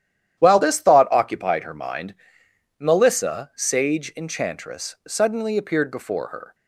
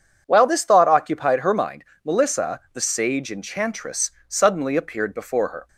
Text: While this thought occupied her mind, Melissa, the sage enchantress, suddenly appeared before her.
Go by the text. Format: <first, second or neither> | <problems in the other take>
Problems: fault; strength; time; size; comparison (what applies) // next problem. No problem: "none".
second | starts louder than the rest; strong; until 1.4 s; 11 dB // skips "the"; at 3.5 s